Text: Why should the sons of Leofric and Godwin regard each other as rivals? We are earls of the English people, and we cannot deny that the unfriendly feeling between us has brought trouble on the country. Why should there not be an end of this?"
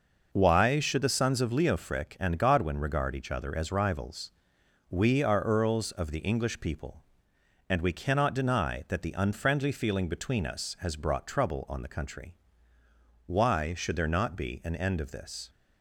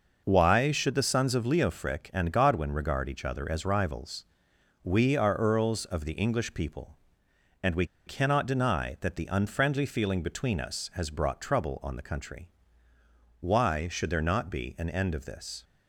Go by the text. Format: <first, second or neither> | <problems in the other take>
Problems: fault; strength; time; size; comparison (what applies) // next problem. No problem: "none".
first | pauses between "we" and "cannot"; slight; at 7.8 s; 0.21 s long